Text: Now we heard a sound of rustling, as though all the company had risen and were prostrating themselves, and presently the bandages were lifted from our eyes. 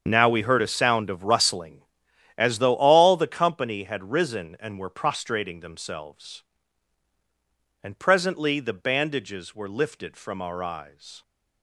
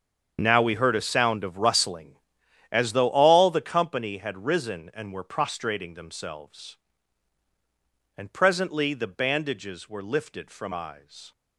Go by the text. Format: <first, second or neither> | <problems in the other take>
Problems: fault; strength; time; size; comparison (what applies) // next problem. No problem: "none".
first | starts louder than the rest; strong; until 1.4 s; 7 dB; strong in the first // skips "our"; at 10.7 s